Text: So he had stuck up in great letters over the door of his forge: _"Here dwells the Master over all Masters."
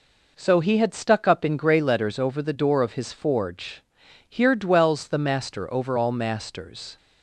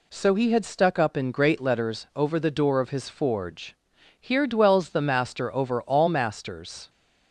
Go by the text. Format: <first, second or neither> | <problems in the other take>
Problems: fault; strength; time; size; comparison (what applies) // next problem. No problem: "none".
second | says "grey" for "great"; at 1.5 s